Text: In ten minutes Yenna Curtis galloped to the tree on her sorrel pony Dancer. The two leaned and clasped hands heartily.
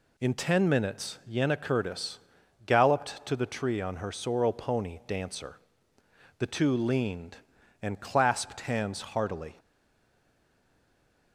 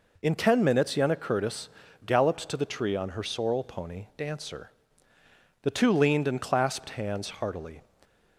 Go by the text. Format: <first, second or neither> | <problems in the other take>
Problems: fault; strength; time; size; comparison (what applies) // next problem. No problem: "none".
second | pauses between "Curtis" and "galloped"; noticeable; at 2.1 s; 0.46 s long; slight in the second // stays silent after the last word; noticeable; from 9.5 s on; 1.8 s long